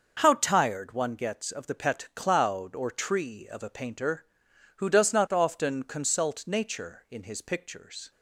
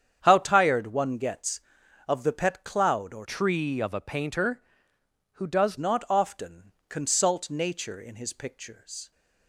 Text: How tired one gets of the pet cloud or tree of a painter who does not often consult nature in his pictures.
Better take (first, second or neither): first